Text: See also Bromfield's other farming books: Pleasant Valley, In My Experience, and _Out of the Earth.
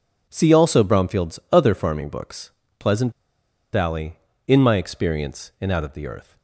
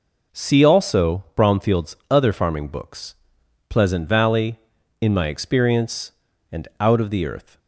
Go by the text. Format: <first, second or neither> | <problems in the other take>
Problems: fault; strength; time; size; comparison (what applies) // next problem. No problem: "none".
second | pauses between "Pleasant" and "Valley"; noticeable; at 3.1 s; 0.61 s long